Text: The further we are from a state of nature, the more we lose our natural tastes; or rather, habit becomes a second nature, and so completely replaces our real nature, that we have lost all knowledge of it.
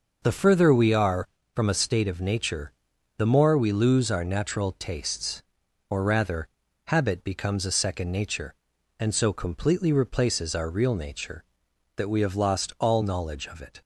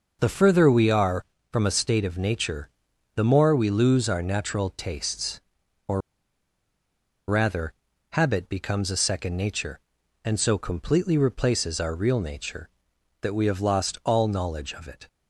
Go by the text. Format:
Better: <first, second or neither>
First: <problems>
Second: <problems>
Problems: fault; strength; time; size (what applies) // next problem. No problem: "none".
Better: first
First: none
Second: pauses between "or" and "rather"; strong; at 6.0 s; 1.2 s long